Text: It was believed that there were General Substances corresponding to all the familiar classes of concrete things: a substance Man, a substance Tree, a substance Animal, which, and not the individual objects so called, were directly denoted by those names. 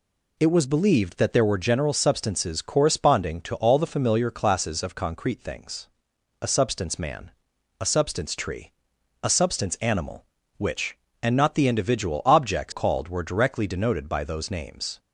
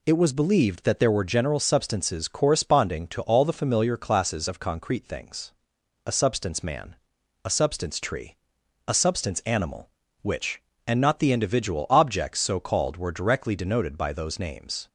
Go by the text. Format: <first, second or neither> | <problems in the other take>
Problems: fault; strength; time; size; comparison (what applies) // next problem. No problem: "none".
second | skips "so"; at 12.7 s